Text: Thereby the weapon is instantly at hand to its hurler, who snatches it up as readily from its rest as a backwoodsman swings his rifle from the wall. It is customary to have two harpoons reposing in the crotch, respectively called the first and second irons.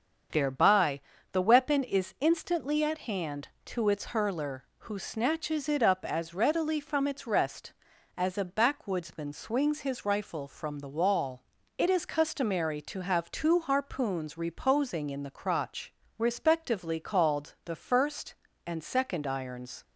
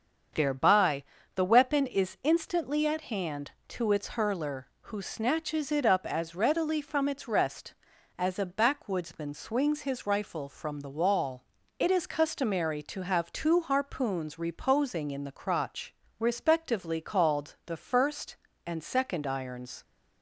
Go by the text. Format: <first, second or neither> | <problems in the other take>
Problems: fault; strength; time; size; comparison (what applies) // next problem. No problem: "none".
neither | starts louder than the rest; the same in both // pauses between "Thereby" and "the"; slight; the same in both